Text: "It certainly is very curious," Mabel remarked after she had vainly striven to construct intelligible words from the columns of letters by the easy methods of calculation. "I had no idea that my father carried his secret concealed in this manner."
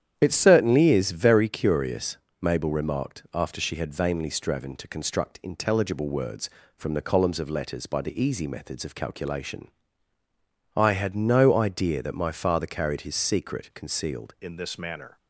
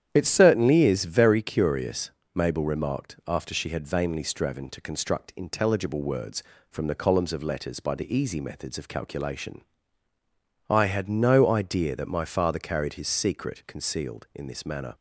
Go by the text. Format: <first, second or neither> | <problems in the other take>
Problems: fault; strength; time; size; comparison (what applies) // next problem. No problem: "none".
second | starts louder than the rest; strong; until 1.1 s; 9.5 dB; strong in the second // changes voice at "in"; from 14.4 s on; 0.7 s long